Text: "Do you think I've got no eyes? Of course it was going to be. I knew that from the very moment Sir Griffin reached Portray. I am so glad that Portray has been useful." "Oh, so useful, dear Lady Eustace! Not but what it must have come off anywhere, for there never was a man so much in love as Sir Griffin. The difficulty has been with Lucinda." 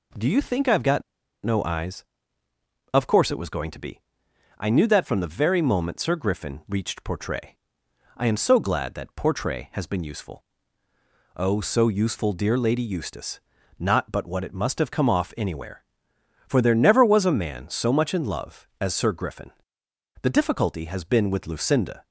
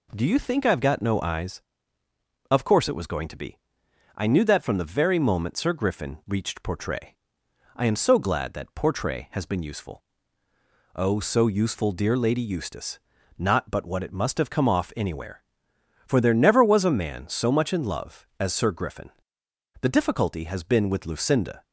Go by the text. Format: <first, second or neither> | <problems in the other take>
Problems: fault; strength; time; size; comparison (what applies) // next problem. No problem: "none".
second | pauses between "got" and "no"; at 1.0 s; 0.41 s long